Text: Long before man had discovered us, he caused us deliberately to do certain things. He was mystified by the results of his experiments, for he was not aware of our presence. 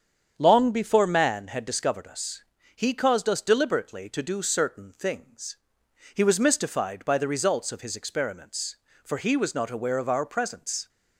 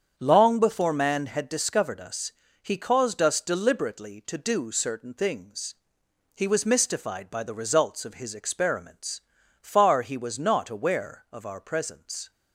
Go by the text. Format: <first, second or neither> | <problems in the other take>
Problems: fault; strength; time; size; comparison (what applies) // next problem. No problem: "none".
first | starts louder than the rest; strong; until 1.1 s; 7.5 dB; strong in the first // says "far" for "for"; at 9.6 s